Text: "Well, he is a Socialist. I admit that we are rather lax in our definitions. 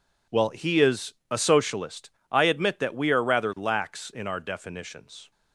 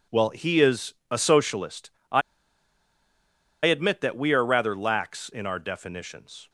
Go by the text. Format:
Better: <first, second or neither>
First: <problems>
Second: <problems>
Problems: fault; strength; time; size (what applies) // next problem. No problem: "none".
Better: first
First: pauses between "is" and "a"; slight; at 1.1 s; 0.16 s long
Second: pauses between "is" and "a"; slight; at 0.9 s; 0.16 s long // pauses between "I" and "admit"; strong; at 2.2 s; 1.4 s long